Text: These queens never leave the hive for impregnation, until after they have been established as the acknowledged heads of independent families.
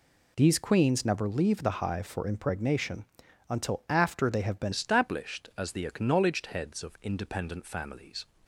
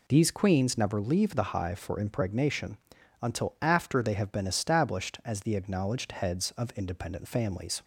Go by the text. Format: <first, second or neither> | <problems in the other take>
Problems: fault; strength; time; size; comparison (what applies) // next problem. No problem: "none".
second | changes voice at "established"; from 4.7 s on; 3.5 s long